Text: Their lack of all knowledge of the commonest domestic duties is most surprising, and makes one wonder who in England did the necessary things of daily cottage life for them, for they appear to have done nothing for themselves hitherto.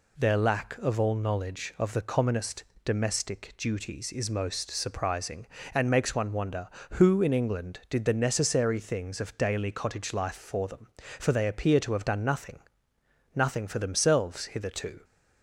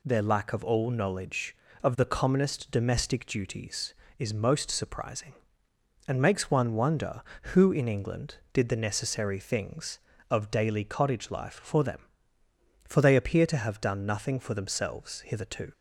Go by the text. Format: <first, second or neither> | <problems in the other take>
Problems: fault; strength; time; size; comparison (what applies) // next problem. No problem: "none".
second | pauses between "commonest" and "domestic"; slight; at 2.6 s; 0.21 s long // says "nothing" twice; at 13.3 s